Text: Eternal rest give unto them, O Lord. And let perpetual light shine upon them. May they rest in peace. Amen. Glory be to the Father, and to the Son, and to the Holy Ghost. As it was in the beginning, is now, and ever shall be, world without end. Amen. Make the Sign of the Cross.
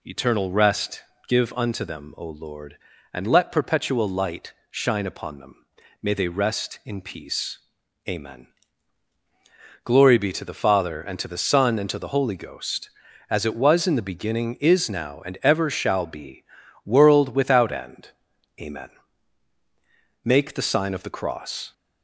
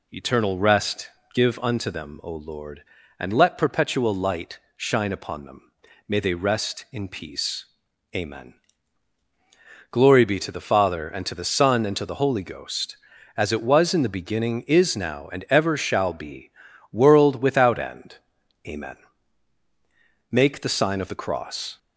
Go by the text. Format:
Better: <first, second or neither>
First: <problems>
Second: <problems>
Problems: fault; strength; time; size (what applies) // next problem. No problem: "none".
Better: neither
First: pauses between "rest" and "give"; slight; at 1.0 s; 0.26 s long // pauses between "light" and "shine"; slight; at 4.5 s; 0.16 s long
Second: pauses between "rest" and "give"; slight; at 1.0 s; 0.25 s long // pauses between "light" and "shine"; slight; at 4.5 s; 0.16 s long